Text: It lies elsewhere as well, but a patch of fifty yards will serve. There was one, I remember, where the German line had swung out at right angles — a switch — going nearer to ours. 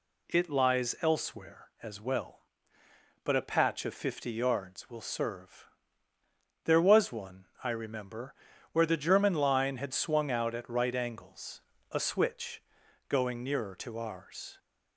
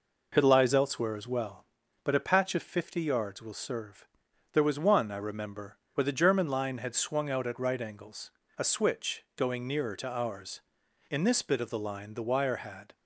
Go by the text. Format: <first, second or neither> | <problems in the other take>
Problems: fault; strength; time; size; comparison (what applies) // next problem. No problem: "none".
first | goes on to say "In this bit of the line the wire had"; strong; from 11.1 s on; 1.8 s long